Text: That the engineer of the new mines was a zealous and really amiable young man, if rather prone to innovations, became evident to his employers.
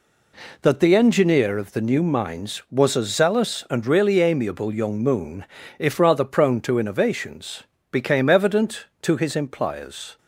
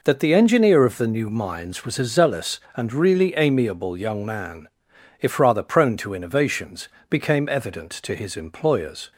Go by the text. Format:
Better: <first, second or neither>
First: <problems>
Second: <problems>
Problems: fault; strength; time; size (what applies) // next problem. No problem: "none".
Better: second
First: says "moon" for "man"; at 5.0 s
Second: none